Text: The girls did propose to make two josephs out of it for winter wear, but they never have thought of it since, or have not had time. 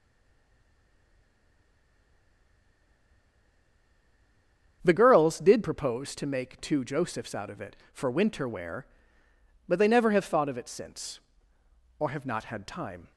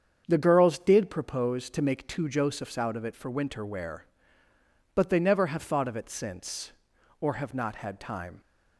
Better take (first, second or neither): second